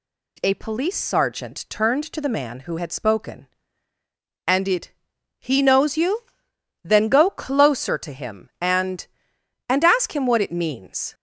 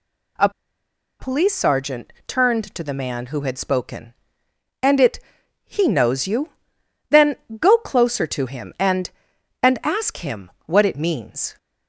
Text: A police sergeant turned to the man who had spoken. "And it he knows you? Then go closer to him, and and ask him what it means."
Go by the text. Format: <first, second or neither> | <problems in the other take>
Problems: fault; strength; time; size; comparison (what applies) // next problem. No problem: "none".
first | pauses between "A" and "police"; noticeable; at 0.4 s; 0.70 s long // pauses between "it" and "he"; noticeable; at 5.1 s; 0.46 s long; noticeable in the first // pauses between "Then" and "go"; slight; at 7.3 s; 0.24 s long // pauses between "him" and "what"; slight; at 10.4 s; 0.16 s long